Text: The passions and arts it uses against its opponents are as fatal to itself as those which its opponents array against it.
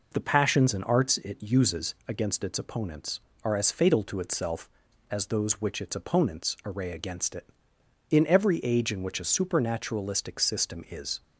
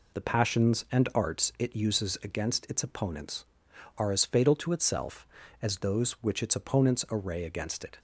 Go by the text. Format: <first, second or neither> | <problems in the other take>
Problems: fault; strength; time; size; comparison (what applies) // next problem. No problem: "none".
second | goes on to say "In every age in which a supernaturalistic system is"; strong; from 8.1 s on; 3.1 s long